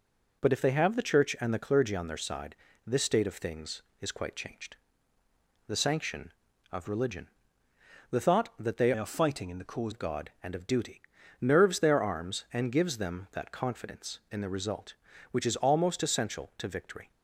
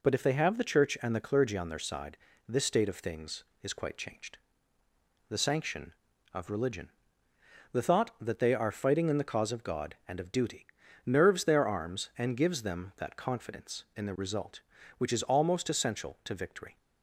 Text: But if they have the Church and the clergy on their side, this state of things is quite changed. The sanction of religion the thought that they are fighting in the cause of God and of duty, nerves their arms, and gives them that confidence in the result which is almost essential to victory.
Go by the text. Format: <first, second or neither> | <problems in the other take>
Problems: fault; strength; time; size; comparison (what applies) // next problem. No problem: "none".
second | pauses between "religion" and "the"; noticeable; at 7.2 s; 0.82 s long; noticeable in the second // changes voice from "are" to "cause"; from 8.9 to 9.9 s; 1.0 s long